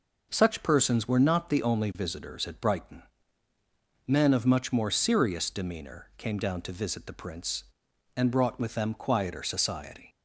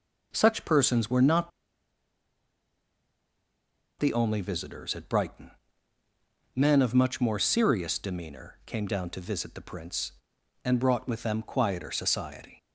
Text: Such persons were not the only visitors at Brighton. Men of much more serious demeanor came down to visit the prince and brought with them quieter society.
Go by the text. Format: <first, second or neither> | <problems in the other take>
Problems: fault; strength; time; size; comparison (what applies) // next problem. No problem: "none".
first | pauses between "not" and "the"; strong; at 1.5 s; 2.5 s long